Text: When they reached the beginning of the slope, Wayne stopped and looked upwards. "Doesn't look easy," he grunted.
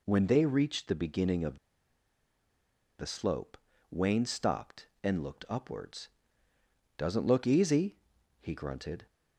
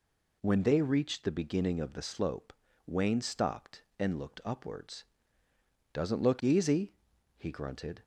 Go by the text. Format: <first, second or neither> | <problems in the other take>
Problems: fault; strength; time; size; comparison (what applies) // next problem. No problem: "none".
second | pauses between "of" and "the"; strong; at 1.5 s; 1.4 s long